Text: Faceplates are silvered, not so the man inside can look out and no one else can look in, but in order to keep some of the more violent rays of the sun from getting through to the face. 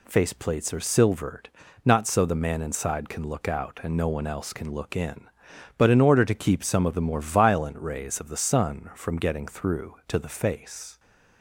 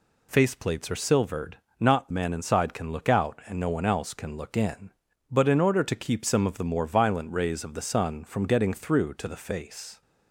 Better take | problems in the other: first | skips "so the"; at 2.1 s

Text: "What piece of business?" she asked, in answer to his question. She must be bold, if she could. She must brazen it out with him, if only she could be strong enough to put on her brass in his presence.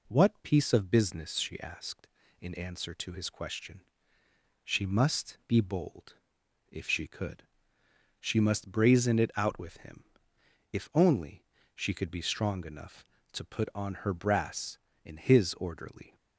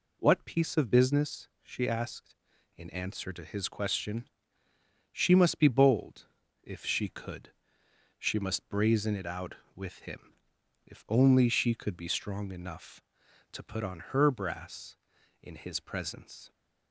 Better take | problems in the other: second | pauses between "only" and "she"; slight; at 11.4 s; 0.30 s long // says "orderly" for "presence"; at 15.5 s

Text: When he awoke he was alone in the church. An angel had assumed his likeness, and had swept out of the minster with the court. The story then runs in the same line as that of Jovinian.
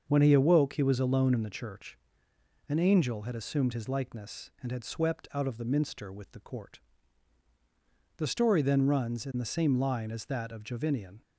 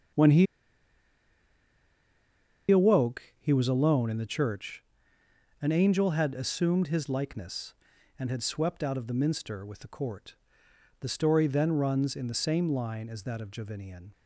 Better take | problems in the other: first | starts louder than the rest; strong; until 3.5 s; 7.5 dB; also in the first // pauses between "he" and "awoke"; strong; at 0.4 s; 2.2 s long // pauses between "awoke" and "he"; slight; at 3.2 s; 0.18 s long

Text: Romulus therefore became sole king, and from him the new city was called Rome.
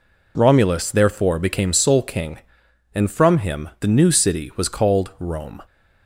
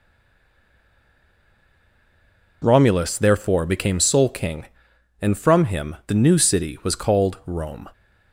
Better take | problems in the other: first | stays silent before the first word; strong; until 2.6 s; 2.6 s long

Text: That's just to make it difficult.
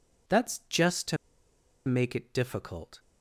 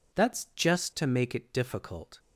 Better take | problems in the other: second | pauses between "to" and "make"; noticeable; at 1.1 s; 0.70 s long

